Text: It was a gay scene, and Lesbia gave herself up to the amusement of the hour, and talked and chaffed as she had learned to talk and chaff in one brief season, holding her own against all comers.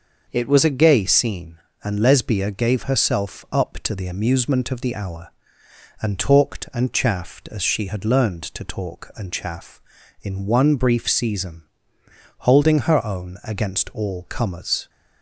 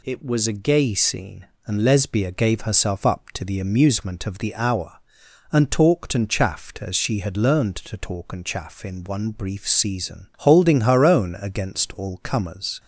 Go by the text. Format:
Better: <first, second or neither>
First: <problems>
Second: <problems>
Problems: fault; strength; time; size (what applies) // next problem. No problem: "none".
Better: neither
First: none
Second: none